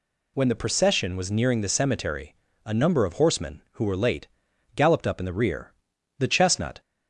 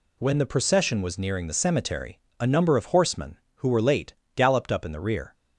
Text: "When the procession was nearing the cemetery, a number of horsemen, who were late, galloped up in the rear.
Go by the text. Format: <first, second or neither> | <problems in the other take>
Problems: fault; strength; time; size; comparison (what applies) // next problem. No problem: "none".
second | goes on to say "The chestnut"; noticeable; from 6.1 s on; 0.62 s long